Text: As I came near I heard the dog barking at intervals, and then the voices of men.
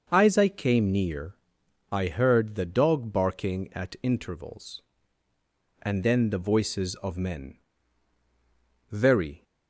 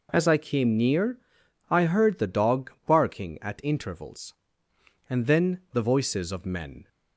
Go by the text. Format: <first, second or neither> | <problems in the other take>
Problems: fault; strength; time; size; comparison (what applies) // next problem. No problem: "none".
second | starts louder than the rest; until 1.1 s; 6 dB // pauses between "near" and "I"; noticeable; at 1.3 s; 0.56 s long; noticeable in the second // goes on to say "Very"; from 8.8 s on; 0.54 s long